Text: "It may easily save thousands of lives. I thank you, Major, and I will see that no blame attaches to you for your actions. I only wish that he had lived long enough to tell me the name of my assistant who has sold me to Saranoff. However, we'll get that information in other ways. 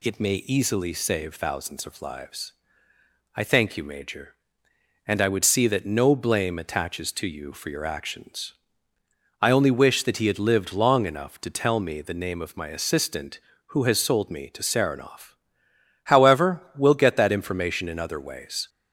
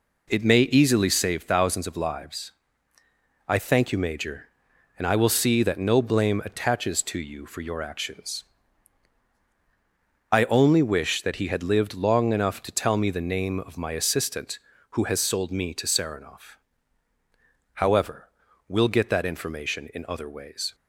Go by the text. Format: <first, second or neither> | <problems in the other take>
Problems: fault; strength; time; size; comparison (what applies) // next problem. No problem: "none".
second | says "would" for "will"; at 5.2 s